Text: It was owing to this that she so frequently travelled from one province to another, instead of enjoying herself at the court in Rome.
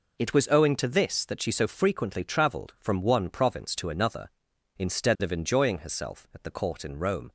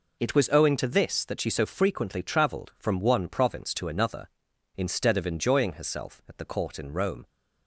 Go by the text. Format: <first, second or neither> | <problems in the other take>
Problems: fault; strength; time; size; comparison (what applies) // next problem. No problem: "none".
neither | none